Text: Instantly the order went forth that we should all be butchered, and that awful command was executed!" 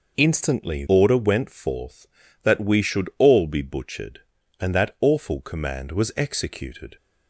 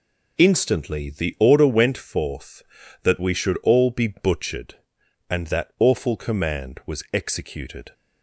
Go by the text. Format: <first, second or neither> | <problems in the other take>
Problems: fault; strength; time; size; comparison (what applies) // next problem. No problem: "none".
second | skips "the"; at 0.8 s